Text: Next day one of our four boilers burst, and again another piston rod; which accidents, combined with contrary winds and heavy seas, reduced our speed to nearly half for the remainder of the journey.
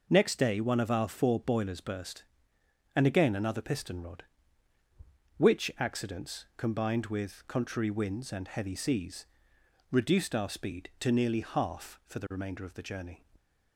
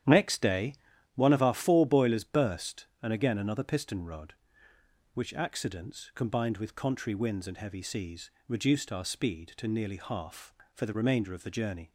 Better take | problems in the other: first | starts louder than the rest; strong; until 1.2 s; 10 dB // pauses between "day" and "one"; at 0.7 s; 0.40 s long

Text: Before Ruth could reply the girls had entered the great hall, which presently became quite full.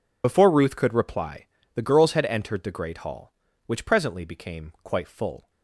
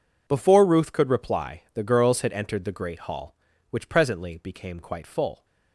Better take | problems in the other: second | loses the start of "Before"; at 0.2 s; 45 ms // pauses between "reply" and "the"; slight; at 1.4 s; 0.30 s long

